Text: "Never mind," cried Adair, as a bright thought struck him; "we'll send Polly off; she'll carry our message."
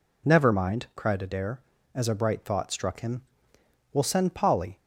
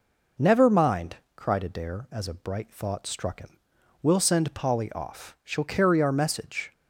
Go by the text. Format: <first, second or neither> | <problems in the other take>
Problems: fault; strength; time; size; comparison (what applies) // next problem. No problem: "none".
second | stops before "off she'll carry our message"; at 4.7 s